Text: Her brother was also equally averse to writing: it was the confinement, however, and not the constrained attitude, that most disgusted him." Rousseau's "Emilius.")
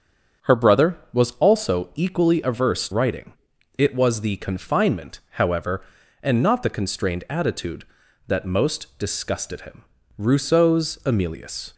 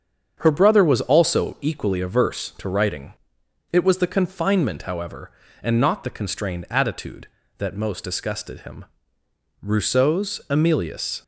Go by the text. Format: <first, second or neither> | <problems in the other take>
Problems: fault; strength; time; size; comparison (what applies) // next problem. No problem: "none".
second | starts louder than the rest; strong; until 1.5 s; 7.5 dB; strong in the second // skips "to"; at 2.8 s